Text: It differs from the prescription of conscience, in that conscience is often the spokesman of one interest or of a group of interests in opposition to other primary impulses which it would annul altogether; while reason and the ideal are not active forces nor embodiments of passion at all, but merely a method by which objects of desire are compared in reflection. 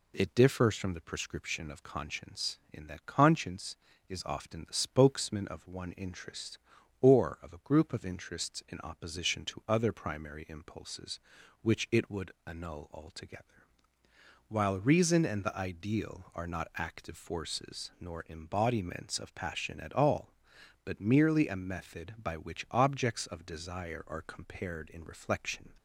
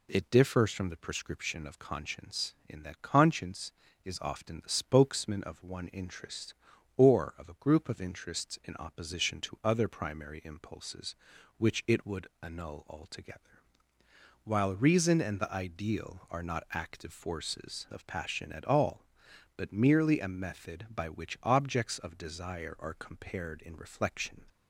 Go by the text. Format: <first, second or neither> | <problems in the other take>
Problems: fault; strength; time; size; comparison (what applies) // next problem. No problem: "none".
first | pauses between "would" and "annul"; slight; at 12.2 s; 0.16 s long; slight in the first // skips "nor embodiments"; at 17.8 s